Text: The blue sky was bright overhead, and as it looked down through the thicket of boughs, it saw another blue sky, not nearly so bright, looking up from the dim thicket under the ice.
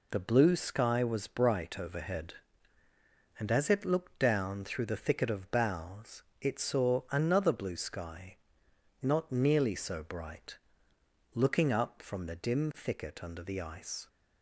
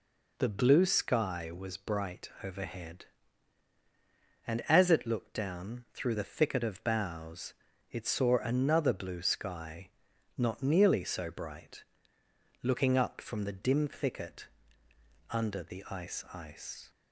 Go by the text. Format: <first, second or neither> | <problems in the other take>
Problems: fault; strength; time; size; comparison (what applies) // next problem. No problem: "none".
first | pauses between "bright" and "overhead"; slight; at 2.2 s; 0.16 s long // pauses between "thicket" and "under"; noticeable; at 14.4 s; 0.82 s long // says "ice" twice; at 16.3 s